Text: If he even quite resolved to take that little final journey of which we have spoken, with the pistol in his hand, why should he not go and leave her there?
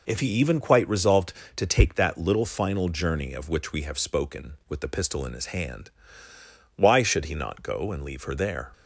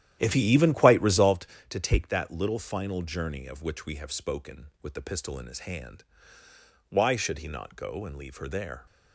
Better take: first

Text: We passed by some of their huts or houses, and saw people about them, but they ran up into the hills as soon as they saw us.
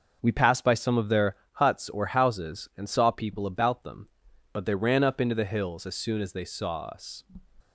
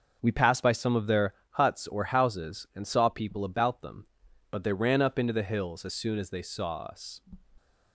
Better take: neither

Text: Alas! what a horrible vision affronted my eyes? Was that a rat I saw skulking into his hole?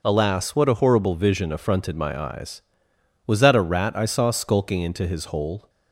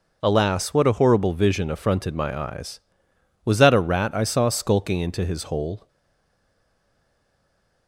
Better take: first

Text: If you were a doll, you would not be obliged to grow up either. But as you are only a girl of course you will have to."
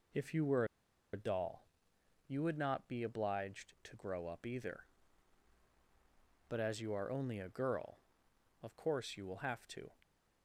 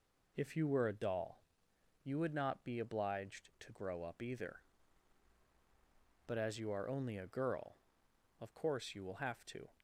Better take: second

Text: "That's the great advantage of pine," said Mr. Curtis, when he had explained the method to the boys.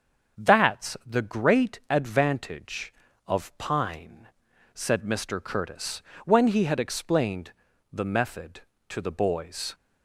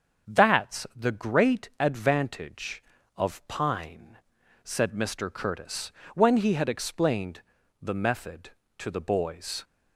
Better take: neither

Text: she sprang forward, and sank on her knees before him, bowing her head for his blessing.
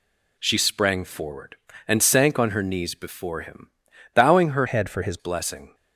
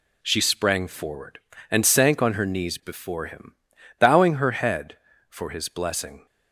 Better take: second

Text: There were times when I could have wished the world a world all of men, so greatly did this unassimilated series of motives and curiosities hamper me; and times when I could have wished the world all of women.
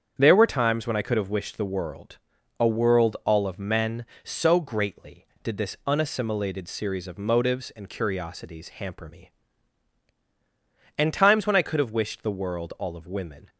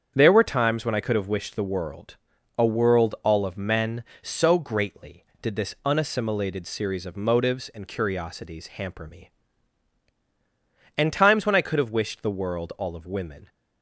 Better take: neither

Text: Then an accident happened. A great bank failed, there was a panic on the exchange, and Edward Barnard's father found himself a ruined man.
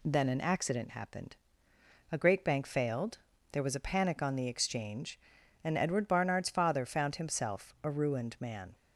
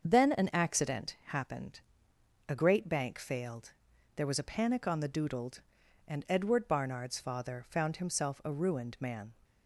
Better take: first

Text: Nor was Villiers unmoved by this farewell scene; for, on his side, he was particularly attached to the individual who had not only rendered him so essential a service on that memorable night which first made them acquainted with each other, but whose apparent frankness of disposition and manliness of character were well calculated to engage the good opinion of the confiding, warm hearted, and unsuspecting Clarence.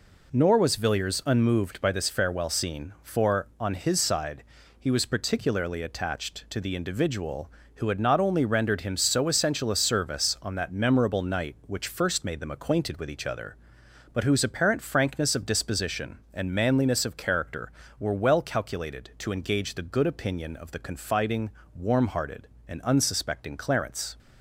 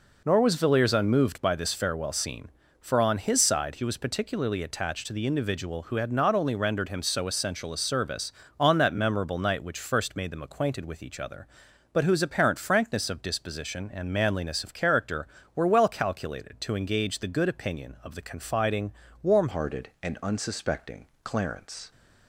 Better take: first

